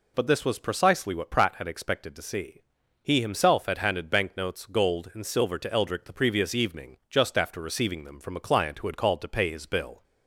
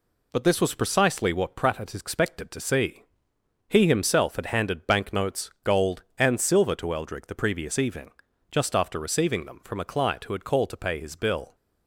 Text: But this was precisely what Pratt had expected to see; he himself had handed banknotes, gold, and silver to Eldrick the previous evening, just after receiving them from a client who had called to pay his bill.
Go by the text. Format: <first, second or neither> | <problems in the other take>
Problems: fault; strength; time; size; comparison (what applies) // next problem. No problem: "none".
neither | none